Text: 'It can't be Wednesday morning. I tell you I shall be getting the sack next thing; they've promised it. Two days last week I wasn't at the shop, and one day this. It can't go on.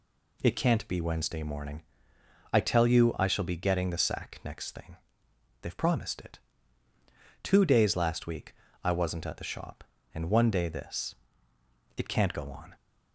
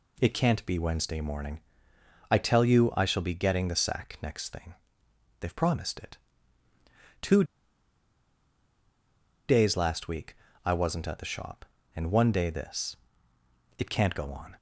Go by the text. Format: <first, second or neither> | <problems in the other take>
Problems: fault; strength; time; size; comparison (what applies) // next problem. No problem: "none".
first | pauses between "Two" and "days"; strong; at 7.4 s; 2.0 s long // pauses between "week" and "I"; slight; at 10.3 s; 0.30 s long; slight in the first